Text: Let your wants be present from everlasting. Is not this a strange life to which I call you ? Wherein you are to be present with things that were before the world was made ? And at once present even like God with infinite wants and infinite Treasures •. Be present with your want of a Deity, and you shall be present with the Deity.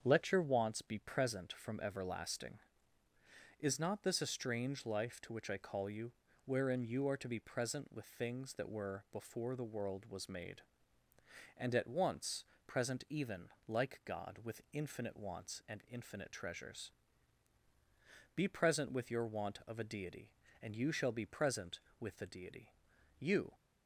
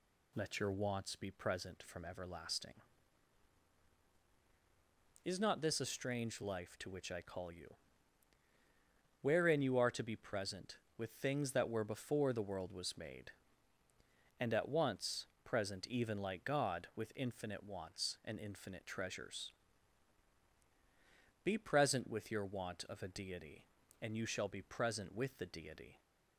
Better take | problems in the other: second | starts louder than the rest; strong; until 1.0 s; 7.5 dB // pauses between "once" and "present"; slight; at 12.4 s; 0.22 s long; slight in the second // pauses between "even" and "like"; slight; at 13.4 s; 0.20 s long // goes on to say "You"; slight; from 23.1 s on; 0.34 s long

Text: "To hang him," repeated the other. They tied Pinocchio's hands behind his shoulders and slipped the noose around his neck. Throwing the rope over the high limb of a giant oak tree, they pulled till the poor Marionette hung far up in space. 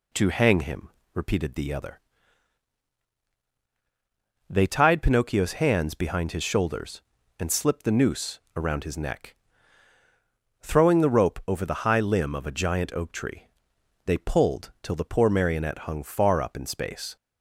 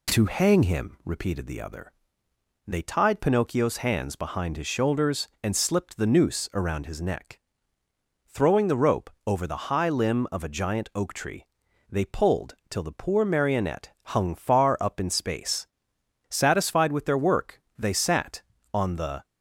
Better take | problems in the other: first | pauses between "rope" and "over"; slight; at 9.1 s; 0.16 s long // pauses between "pulled" and "till"; slight; at 12.5 s; 0.16 s long // goes on to say "Satisfied with their work they sat on the"; strong; from 16.3 s on; 2.9 s long

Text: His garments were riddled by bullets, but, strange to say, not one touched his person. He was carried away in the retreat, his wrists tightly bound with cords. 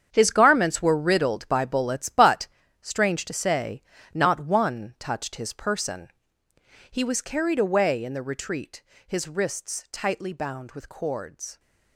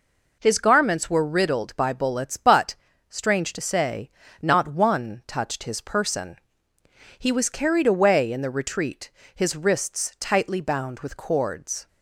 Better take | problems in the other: second | gets quieter; strong; throughout; 12 dB

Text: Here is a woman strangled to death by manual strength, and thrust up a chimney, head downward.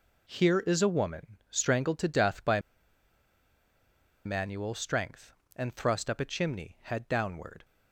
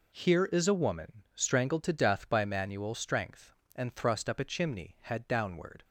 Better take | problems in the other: second | pauses between "by" and "manual"; strong; at 2.5 s; 1.6 s long

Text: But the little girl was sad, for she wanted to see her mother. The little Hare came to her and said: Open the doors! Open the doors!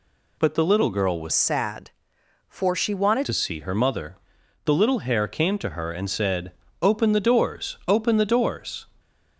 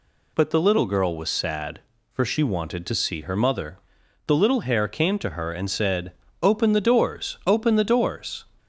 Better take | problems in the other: second | changes voice from "sad" to "wanted"; from 1.3 to 3.2 s; 1.9 s long

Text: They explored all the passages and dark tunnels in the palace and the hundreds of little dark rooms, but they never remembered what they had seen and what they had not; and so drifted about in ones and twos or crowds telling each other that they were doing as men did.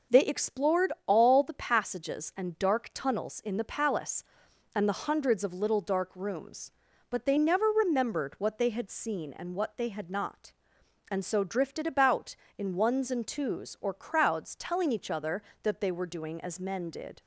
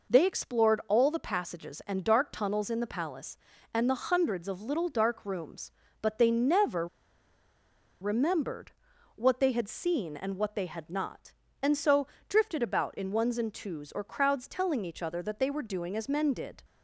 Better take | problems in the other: first | pauses between "never" and "remembered"; at 6.8 s; 1.1 s long // pauses between "remembered" and "what"; noticeable; at 8.7 s; 0.46 s long // pauses between "so" and "drifted"; slight; at 12.0 s; 0.22 s long

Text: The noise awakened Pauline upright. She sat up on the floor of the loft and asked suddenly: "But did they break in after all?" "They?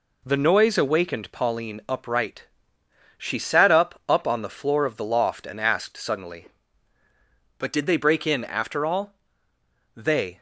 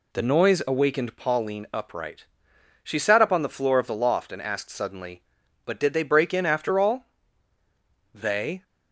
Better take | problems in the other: second | says "up" twice; at 4.0 s

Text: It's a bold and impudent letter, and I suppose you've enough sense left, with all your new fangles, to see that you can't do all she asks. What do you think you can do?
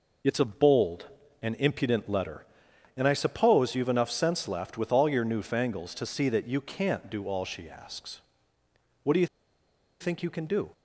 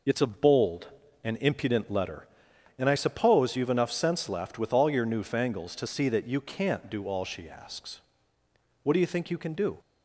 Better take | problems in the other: second | pauses between "you" and "think"; noticeable; at 9.2 s; 0.74 s long

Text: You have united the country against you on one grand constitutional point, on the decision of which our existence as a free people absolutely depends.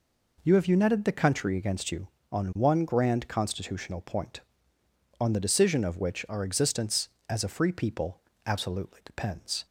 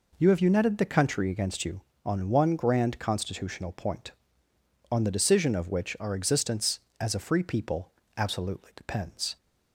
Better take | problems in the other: neither | pauses between "people" and "absolutely"; slight; the same in both

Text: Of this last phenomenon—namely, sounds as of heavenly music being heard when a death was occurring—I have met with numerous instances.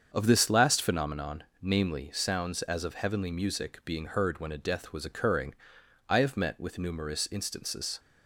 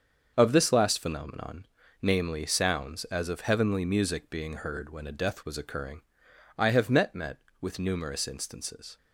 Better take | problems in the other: first | starts louder than the rest; until 1.3 s; 7 dB; strong in the first // says "met" twice; at 7.1 s

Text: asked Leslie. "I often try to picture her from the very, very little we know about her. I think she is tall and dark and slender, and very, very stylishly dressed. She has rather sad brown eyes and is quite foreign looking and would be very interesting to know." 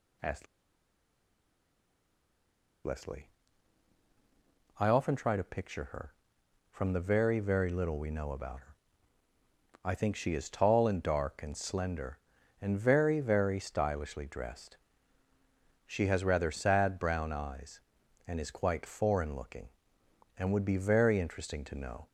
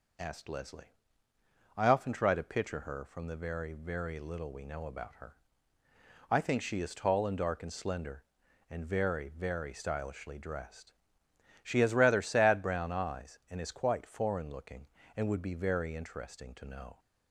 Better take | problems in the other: second | pauses between "asked" and "Leslie"; strong; at 0.4 s; 2.3 s long

